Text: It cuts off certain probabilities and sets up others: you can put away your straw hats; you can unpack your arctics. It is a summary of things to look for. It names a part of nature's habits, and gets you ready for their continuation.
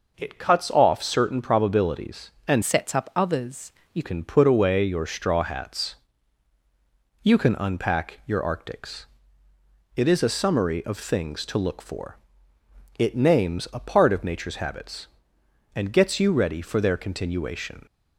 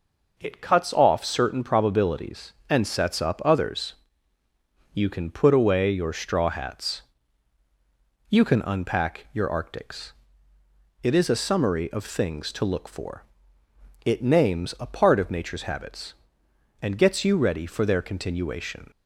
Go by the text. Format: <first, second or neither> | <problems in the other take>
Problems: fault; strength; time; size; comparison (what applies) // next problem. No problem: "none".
second | changes voice from "sets" to "you"; from 2.6 to 4.0 s; 1.4 s long